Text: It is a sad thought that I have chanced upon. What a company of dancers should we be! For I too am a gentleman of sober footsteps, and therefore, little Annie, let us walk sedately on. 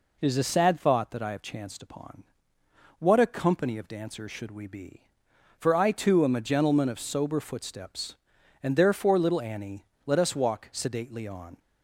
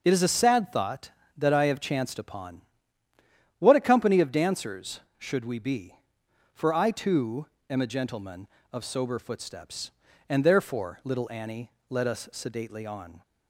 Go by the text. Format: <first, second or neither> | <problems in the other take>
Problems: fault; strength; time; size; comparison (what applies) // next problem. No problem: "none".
first | pauses between "too" and "am"; slight; at 7.4 s; 0.24 s long // skips "walk"; at 12.2 s